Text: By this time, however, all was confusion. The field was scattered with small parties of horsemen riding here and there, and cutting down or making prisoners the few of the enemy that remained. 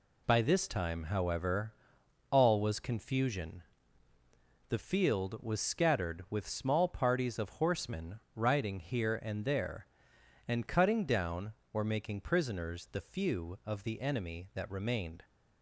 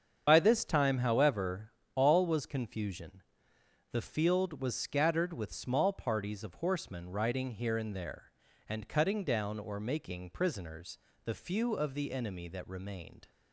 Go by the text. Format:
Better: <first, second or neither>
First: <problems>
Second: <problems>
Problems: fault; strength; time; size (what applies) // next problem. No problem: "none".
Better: first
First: none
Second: loses the start of "By"; at 0.2 s; 55 ms // starts louder than the rest; strong; until 1.2 s; 7.5 dB // pauses between "prisoners" and "the"; slight; at 10.9 s; 0.26 s long